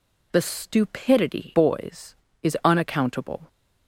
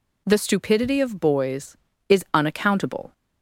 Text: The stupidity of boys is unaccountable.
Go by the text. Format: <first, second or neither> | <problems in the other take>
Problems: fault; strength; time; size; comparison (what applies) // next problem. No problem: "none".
second | skips "of"; at 1.5 s